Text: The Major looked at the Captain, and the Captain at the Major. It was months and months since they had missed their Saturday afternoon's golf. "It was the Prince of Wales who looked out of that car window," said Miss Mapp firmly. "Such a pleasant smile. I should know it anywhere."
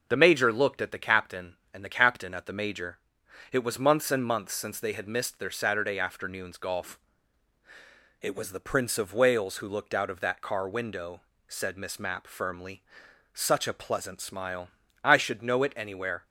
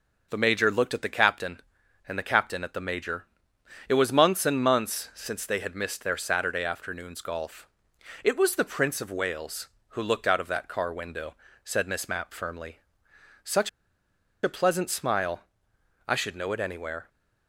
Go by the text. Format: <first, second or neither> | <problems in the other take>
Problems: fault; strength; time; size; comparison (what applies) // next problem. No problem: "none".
first | pauses between "Such" and "a"; noticeable; at 13.6 s; 0.74 s long